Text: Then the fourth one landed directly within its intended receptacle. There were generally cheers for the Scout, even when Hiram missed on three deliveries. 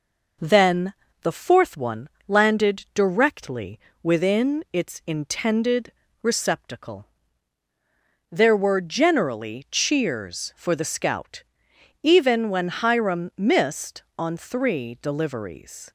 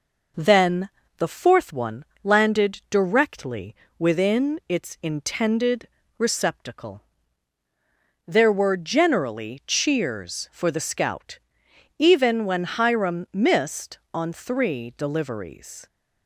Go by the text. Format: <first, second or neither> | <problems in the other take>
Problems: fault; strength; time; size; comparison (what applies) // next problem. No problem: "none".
neither | pauses between "Then" and "the"; slight; the same in both // pauses between "one" and "landed"; slight; the same in both // pauses between "directly" and "within"; slight; the same in both // pauses between "intended" and "receptacle"; slight; the same in both